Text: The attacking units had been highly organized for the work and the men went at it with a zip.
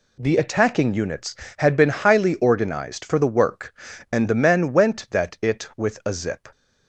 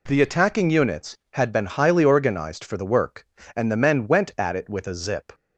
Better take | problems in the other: second | says "that" for "at"; at 5.1 s

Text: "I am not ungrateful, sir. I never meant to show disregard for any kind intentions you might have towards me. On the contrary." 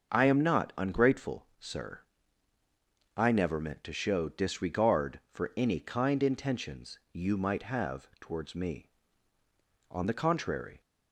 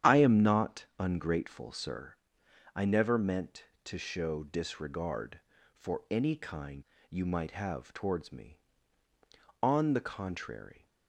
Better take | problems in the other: first | starts louder than the rest; strong; until 1.1 s; 10 dB; also in the first // skips "intentions"; at 6.9 s

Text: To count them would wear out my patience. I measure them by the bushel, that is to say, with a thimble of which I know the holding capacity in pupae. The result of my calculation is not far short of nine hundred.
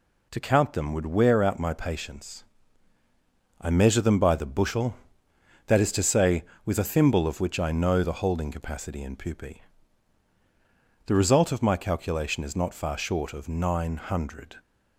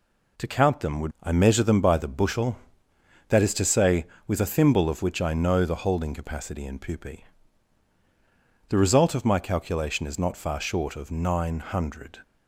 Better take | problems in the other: first | skips "wear out my patience"; at 1.1 s

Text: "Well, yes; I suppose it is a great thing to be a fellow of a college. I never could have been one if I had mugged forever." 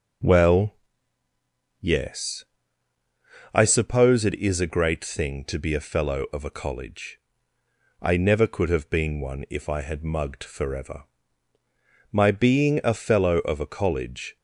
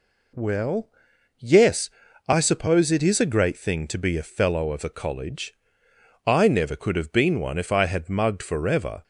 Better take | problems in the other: second | goes on to say "My being a fellow of a college"; strong; from 12.1 s on; 2.2 s long

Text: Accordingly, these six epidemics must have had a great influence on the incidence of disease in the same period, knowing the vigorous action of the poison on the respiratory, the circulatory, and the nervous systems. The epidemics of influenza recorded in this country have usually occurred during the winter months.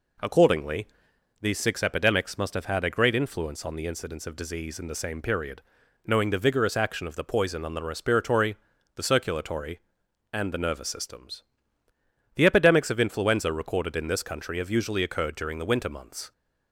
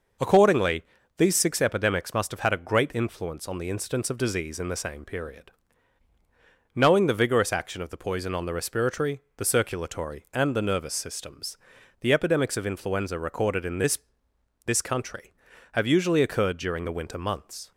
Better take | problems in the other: first | says "this" twice; at 14.6 s

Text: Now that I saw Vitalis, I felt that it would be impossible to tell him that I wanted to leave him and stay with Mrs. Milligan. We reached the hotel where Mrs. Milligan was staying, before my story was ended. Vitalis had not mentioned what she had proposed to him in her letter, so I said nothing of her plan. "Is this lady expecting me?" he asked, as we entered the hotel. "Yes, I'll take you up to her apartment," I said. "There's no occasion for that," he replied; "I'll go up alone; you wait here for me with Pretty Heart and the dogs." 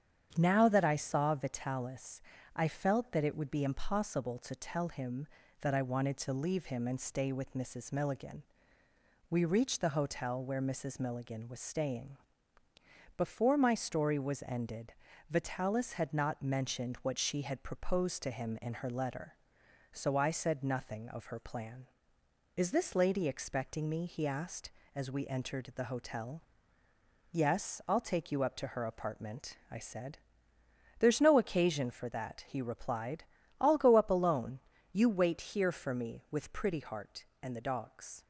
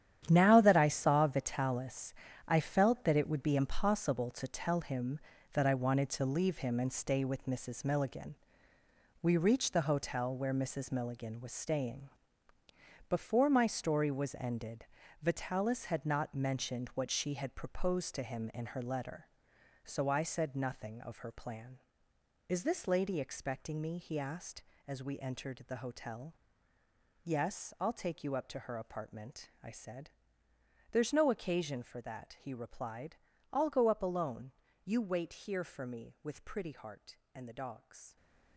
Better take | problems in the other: first | gets quieter; strong; throughout; 11.5 dB // starts louder than the rest; strong; until 1.3 s; 10 dB; strong in the first

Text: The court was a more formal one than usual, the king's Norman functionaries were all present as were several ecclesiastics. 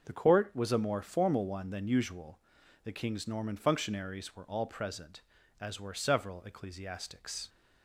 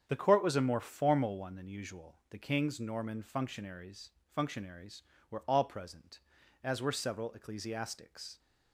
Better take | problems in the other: first | starts louder than the rest; strong; until 1.0 s; 8 dB; also in the first // says "functionaries" twice; at 4.2 s

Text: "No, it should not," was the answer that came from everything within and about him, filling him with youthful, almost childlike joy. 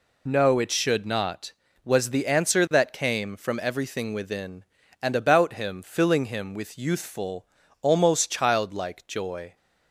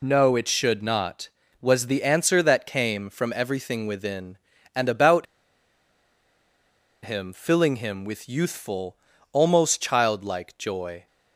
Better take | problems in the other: first | pauses between "about" and "him"; strong; at 5.2 s; 1.7 s long

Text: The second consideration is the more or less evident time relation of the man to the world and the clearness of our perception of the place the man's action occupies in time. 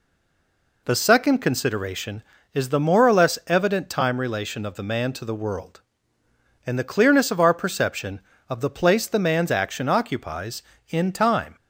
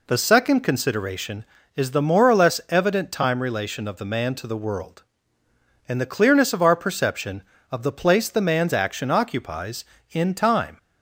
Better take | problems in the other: second | stays silent before the first word; slight; until 0.8 s; 0.8 s long

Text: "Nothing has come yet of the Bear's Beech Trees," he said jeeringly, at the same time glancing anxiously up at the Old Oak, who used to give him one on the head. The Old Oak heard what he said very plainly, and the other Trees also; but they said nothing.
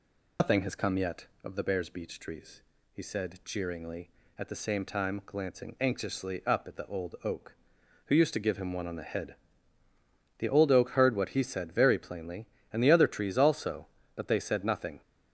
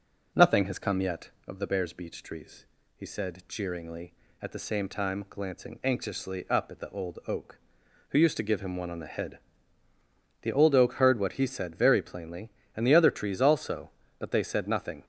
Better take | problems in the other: second | loses the start of "Nothing"; at 0.3 s; 90 ms

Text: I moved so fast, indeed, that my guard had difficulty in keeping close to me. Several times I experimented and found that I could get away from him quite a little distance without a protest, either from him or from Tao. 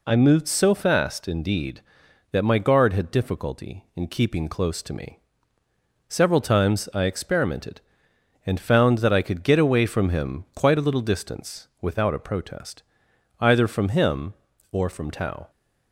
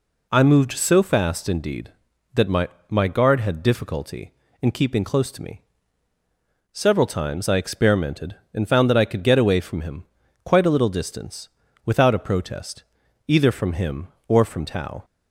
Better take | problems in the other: first | says "my" twice; at 2.8 s // pauses between "him" and "quite"; at 10.0 s; 0.40 s long // pauses between "distance" and "without"; slight; at 11.4 s; 0.36 s long

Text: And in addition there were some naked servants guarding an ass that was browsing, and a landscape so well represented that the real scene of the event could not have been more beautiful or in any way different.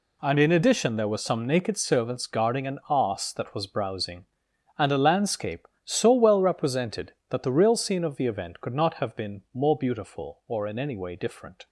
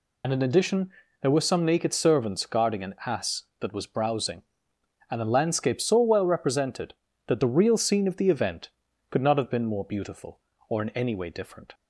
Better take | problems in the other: first | loses the start of "And"; at 0.2 s; 50 ms // pauses between "addition" and "there"; slight; at 0.8 s; 0.32 s long

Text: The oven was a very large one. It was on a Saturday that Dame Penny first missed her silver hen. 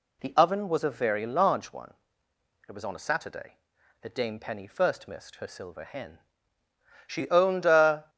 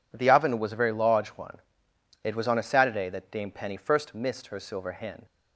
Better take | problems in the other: second | goes on to say "She owned a"; noticeable; from 7.0 s on; 1.0 s long

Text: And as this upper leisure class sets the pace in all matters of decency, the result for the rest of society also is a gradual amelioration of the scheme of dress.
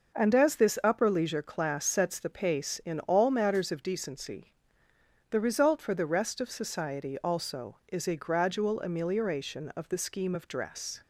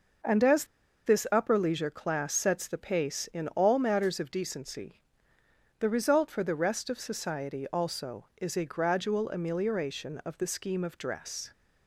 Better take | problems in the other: first | pauses between "as" and "this"; at 0.6 s; 0.40 s long

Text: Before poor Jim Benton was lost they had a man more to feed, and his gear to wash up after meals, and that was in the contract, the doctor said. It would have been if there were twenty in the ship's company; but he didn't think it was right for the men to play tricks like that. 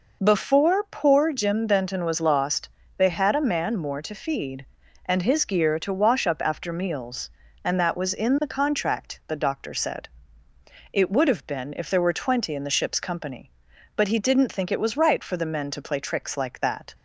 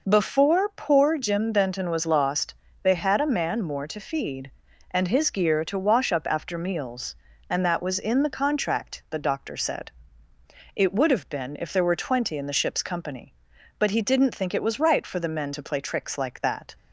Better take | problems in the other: neither | pauses between "lost" and "they"; slight; the same in both

